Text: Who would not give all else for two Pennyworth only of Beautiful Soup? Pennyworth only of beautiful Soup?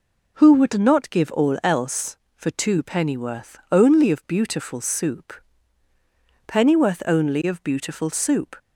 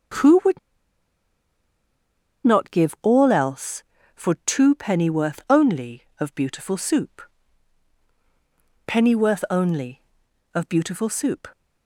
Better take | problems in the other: first | starts louder than the rest; until 3.1 s; 7 dB // pauses between "would" and "not"; strong; at 0.5 s; 1.8 s long

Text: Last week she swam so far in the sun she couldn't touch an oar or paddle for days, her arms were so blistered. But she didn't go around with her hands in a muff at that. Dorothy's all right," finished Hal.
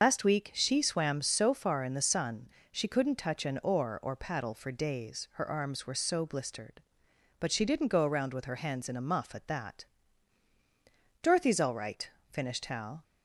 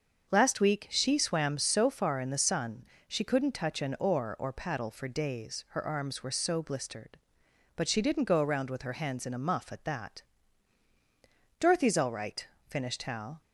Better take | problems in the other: second | loses the start of "Last"; at 0.0 s; 80 ms // starts louder than the rest; until 1.0 s; 6 dB; also in the second // pauses between "sun" and "she"; slight; at 2.4 s; 0.24 s long; slight in the second

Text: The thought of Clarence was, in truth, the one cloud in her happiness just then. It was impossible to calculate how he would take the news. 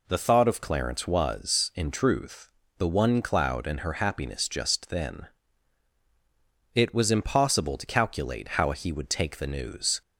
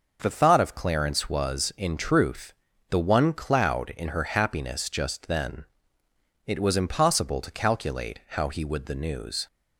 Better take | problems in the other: first | starts louder than the rest; until 1.2 s; 6 dB // skips "take"; at 8.8 s

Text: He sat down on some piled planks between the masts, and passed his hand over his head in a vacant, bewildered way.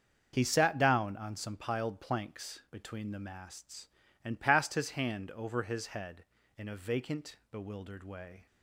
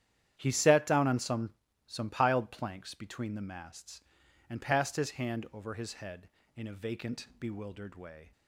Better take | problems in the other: first | starts louder than the rest; strong; until 1.4 s; 10.5 dB; also in the first // says "some" twice; at 1.8 s

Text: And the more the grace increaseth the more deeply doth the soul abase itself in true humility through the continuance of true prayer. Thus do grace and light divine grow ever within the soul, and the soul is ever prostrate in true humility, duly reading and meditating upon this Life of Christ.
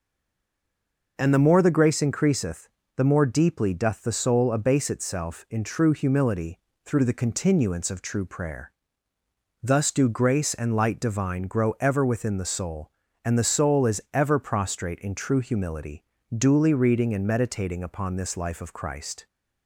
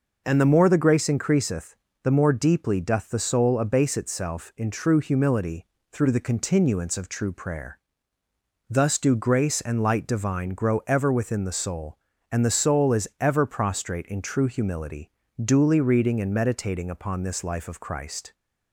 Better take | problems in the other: second | stays silent before the first word; noticeable; until 1.1 s; 1.1 s long // pauses between "increaseth" and "the"; slight; at 2.6 s; 0.28 s long; slight in the second // pauses between "humility" and "through"; slight; at 6.5 s; 0.28 s long; slight in the second

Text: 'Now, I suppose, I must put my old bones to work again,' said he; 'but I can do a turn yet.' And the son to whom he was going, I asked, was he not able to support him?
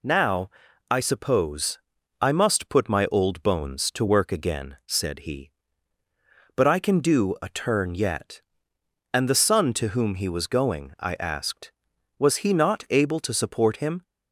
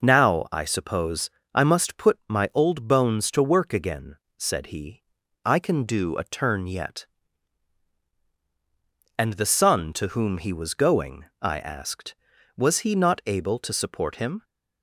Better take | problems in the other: first | skips "but"; at 5.2 s

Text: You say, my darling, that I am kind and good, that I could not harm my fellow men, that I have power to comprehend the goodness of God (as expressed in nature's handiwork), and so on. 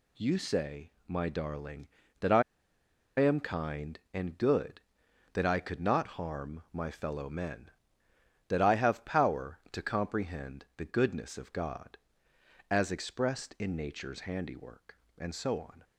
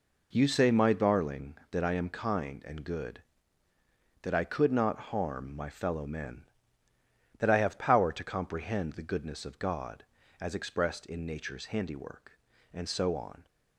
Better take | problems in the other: second | pauses between "I" and "am"; noticeable; at 2.4 s; 0.76 s long

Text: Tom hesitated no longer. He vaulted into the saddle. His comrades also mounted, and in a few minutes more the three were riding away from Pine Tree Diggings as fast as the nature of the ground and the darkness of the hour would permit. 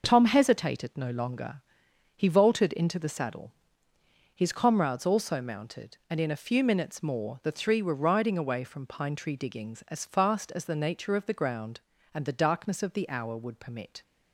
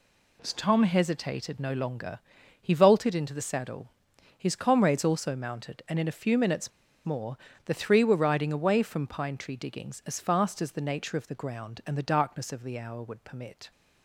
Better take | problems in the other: first | pauses between "minutes" and "more"; slight; at 6.7 s; 0.36 s long // pauses between "more" and "the"; slight; at 7.3 s; 0.30 s long

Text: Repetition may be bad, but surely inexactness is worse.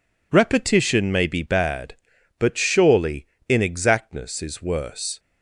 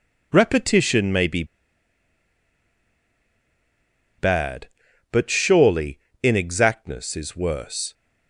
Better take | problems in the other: first | pauses between "be" and "bad"; strong; at 1.4 s; 2.7 s long // pauses between "surely" and "inexactness"; slight; at 5.9 s; 0.24 s long; slight in the first

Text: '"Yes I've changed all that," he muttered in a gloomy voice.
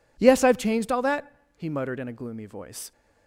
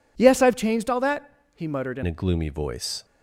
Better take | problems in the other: first | changes voice at "a"; from 2.0 s on; 1.0 s long

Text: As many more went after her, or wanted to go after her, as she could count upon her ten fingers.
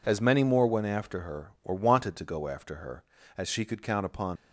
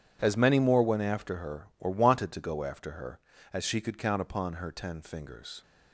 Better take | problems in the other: second | stops before "her ten fingers"; at 4.3 s

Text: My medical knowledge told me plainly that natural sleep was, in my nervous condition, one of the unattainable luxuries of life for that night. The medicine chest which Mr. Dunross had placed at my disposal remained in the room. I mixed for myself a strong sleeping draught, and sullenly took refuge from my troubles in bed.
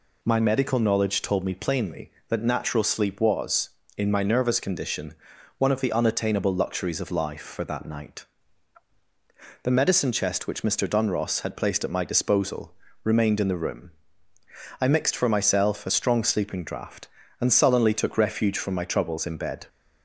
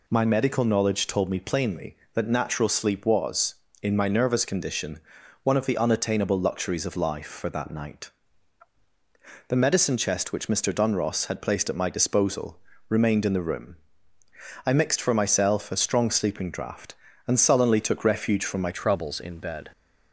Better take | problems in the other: first | pauses between "disposal" and "remained"; slight; at 12.5 s; 0.30 s long; slight in the first // changes voice at "troubles"; from 18.7 s on; 1.0 s long

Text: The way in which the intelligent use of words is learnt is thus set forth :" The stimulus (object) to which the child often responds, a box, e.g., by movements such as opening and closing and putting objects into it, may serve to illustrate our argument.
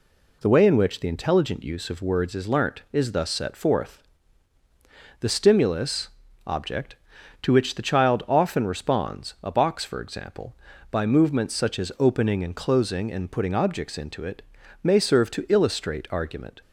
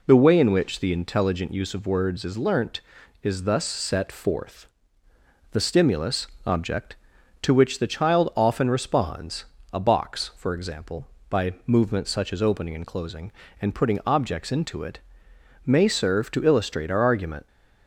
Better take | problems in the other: second | skips "our"; at 16.0 s

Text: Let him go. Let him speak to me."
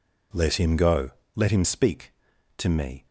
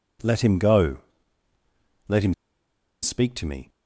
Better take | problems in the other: first | pauses between "him" and "speak"; noticeable; at 2.3 s; 0.68 s long

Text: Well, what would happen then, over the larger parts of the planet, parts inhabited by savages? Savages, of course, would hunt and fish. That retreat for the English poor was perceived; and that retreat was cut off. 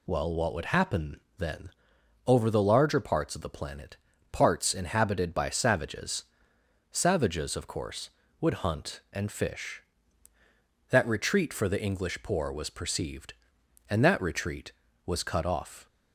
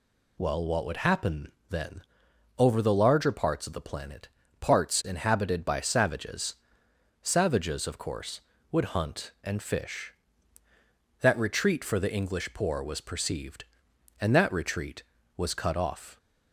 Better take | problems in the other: neither | pauses between "happen" and "then"; slight; the same in both

